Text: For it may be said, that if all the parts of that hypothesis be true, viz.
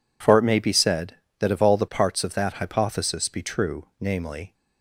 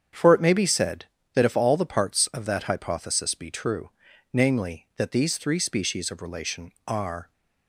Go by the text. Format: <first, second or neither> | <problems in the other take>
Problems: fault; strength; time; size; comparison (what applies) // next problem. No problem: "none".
first | starts louder than the rest; strong; until 1.4 s; 8 dB // goes on to say "that these three species of relation are"; strong; from 4.9 s on; 2.3 s long